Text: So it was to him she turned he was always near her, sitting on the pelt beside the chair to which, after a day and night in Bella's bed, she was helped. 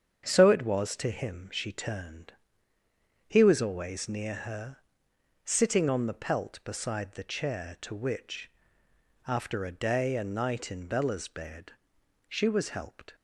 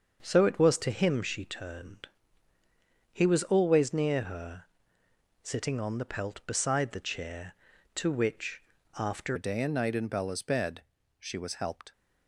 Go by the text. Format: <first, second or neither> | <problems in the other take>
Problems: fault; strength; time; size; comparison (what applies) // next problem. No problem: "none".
first | starts louder than the rest; until 1.2 s; 6.5 dB; strong in the first // pauses between "turned" and "he"; at 2.0 s; 1.0 s long; noticeable in the first // changes voice at "a"; from 9.3 s on; 2.6 s long